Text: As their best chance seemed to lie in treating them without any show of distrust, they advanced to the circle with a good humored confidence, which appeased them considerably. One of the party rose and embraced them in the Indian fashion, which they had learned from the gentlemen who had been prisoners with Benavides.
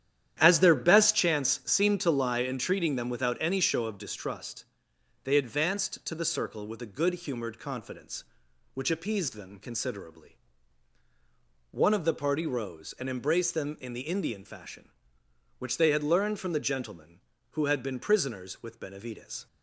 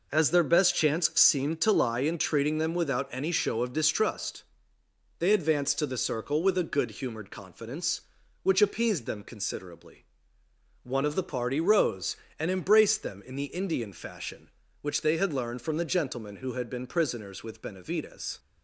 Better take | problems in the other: second | starts louder than the rest; strong; until 1.2 s; 11 dB

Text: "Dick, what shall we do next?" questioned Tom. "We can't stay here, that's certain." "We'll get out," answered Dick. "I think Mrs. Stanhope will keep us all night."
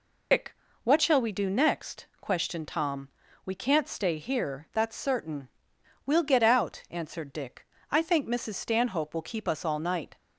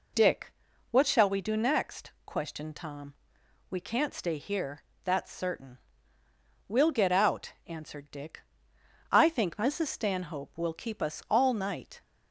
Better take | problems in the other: second | loses the start of "Dick"; at 0.3 s; 105 ms

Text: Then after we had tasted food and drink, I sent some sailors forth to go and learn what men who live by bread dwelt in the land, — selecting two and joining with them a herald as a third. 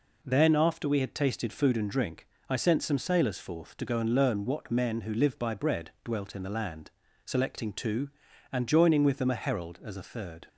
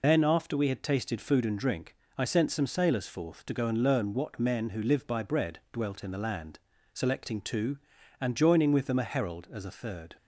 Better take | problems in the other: first | loses the start of "Then"; at 0.0 s; 115 ms

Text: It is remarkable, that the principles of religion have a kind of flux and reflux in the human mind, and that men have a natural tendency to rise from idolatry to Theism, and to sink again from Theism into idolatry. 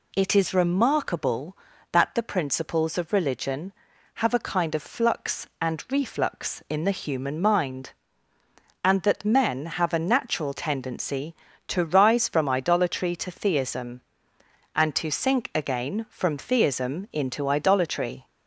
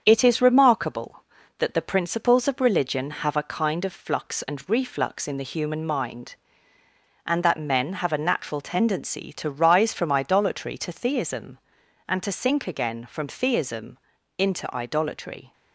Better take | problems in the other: first | gets quieter; throughout; 3.5 dB // pauses between "Theism" and "into"; at 13.9 s; 0.40 s long

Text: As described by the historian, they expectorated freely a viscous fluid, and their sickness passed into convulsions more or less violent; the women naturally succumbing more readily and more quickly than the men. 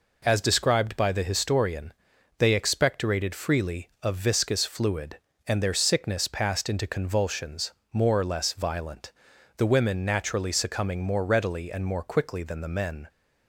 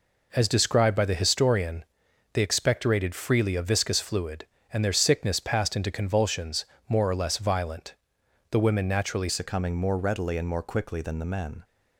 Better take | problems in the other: first | pauses between "convulsions" and "more"; slight; at 6.6 s; 0.22 s long; slight in the first // changes voice at "succumbing"; from 9.2 s on; 2.4 s long

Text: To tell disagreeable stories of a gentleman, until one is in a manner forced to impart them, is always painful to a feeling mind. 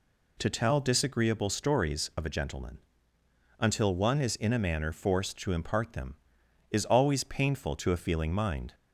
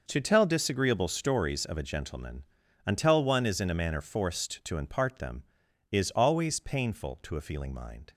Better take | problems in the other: neither | none

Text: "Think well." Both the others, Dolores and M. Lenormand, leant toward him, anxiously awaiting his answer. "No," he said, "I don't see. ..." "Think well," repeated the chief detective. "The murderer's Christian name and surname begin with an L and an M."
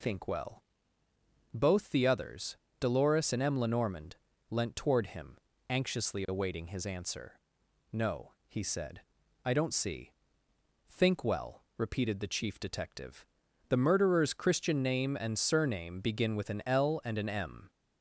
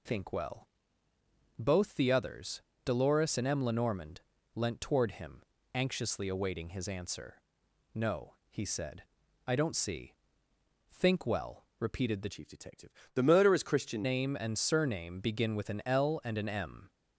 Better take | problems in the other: first | changes voice from "chief" to "Christian"; from 12.3 to 14.0 s; 1.7 s long

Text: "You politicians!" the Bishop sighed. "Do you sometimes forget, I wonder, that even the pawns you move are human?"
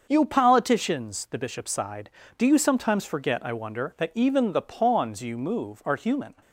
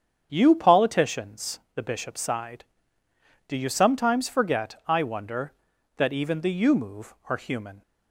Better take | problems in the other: first | starts louder than the rest; strong; until 1.3 s; 7.5 dB; also in the first // skips "pawns"; at 6.5 s

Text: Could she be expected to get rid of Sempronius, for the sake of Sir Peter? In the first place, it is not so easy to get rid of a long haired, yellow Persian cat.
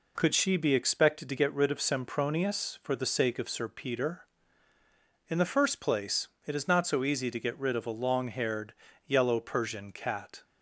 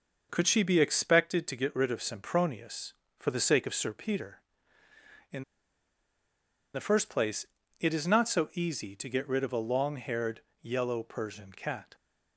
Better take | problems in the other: first | pauses between "In" and "the"; strong; at 5.4 s; 1.3 s long

